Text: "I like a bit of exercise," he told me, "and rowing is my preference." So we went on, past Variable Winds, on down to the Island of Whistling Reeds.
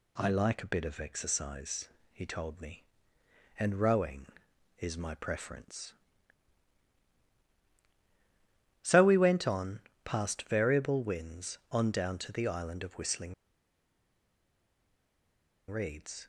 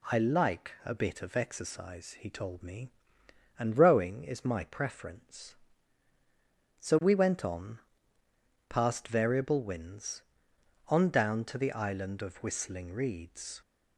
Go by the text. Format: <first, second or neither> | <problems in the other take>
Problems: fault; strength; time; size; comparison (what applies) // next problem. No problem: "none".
second | pauses between "Whistling" and "Reeds"; strong; at 13.3 s; 2.3 s long